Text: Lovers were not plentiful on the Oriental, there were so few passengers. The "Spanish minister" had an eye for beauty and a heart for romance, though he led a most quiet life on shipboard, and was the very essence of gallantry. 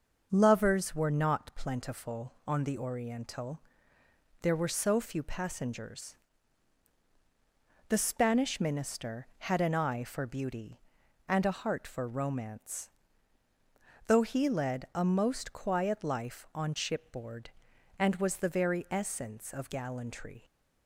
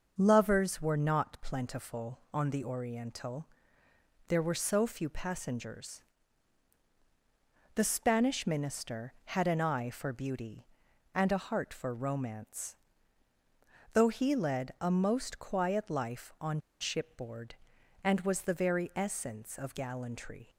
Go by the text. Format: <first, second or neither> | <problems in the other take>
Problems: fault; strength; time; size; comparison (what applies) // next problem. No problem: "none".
first | starts louder than the rest; noticeable; until 1.1 s; 6 dB; noticeable in the first // pauses between "on" and "shipboard"; slight; at 16.5 s; 0.20 s long